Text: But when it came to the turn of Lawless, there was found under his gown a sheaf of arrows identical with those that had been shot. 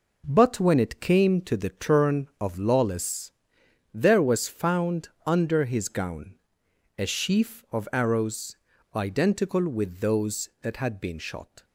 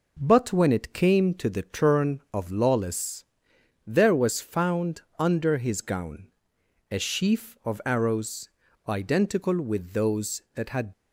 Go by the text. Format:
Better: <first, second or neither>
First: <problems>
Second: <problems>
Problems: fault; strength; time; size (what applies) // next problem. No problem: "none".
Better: first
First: pauses between "found" and "under"; slight; at 5.0 s; 0.18 s long // pauses between "gown" and "a"; noticeable; at 6.3 s; 0.62 s long // pauses between "arrows" and "identical"; at 8.5 s; 0.40 s long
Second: pauses between "found" and "under"; slight; at 5.0 s; 0.18 s long // pauses between "gown" and "a"; noticeable; at 6.2 s; 0.62 s long // pauses between "arrows" and "identical"; at 8.4 s; 0.40 s long // stops before "been shot"; at 10.9 s